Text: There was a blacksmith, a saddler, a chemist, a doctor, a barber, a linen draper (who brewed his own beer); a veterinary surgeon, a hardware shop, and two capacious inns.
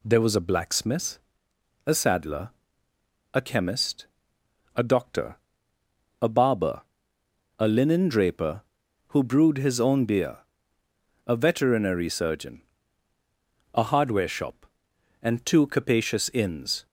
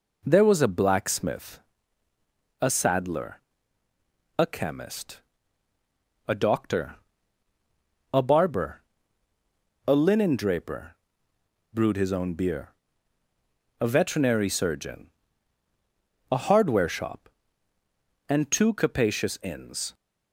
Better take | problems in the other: first | skips "who"; at 11.3 s

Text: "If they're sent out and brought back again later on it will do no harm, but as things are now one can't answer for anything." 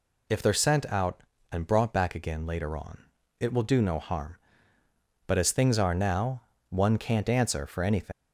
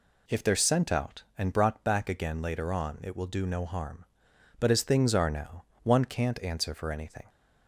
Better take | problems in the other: second | pauses between "on" and "it"; slight; at 3.0 s; 0.36 s long // pauses between "now" and "one"; slight; at 6.4 s; 0.28 s long; slight in the second // leaves "anything" unfinished; at 8.1 s; 115 ms

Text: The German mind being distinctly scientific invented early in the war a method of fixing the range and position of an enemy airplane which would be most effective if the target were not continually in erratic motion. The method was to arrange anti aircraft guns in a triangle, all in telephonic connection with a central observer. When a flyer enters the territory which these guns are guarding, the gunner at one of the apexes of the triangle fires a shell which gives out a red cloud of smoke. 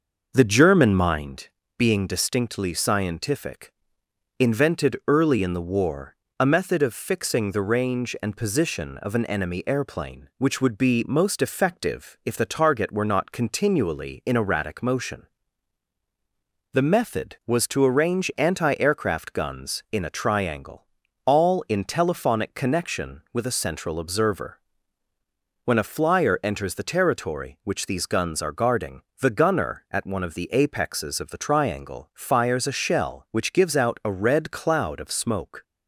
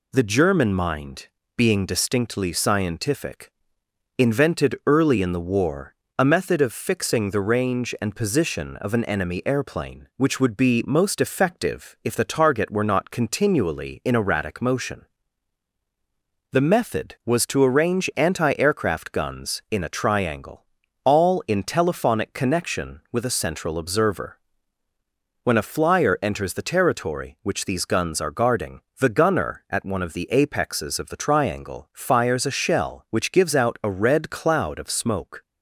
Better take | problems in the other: second | starts louder than the rest; noticeable; until 1.4 s; 6 dB // pauses between "mind" and "being"; slight; at 1.4 s; 0.30 s long; slight in the second // pauses between "scientific" and "invented"; noticeable; at 3.7 s; 0.66 s long; noticeable in the second // pauses between "war" and "a"; slight; at 6.1 s; 0.24 s long; slight in the second

